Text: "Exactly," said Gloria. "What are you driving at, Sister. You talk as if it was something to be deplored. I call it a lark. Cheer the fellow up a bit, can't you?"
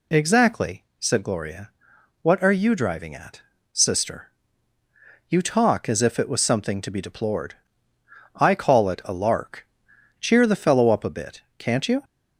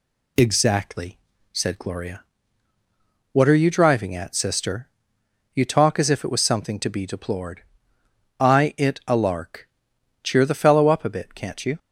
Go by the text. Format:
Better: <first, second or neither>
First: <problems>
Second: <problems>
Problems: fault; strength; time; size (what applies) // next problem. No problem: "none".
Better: first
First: none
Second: skips "call"; at 8.7 s